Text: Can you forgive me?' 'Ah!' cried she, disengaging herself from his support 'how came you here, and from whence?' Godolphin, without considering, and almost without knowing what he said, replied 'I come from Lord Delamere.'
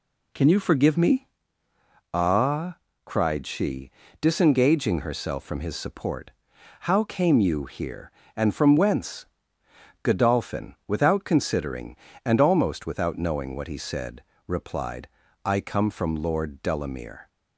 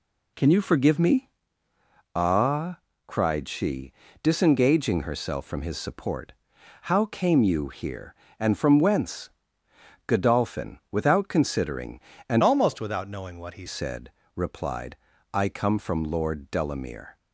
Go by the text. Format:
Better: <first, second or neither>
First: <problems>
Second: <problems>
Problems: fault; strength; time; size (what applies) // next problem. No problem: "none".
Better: first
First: pauses between "support" and "how"; noticeable; at 6.2 s; 0.50 s long // pauses between "replied" and "I"; slight; at 15.0 s; 0.36 s long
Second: pauses between "support" and "how"; noticeable; at 6.3 s; 0.50 s long // changes voice from "almost" to "he"; from 12.4 to 13.6 s; 1.2 s long // pauses between "replied" and "I"; slight; at 14.9 s; 0.36 s long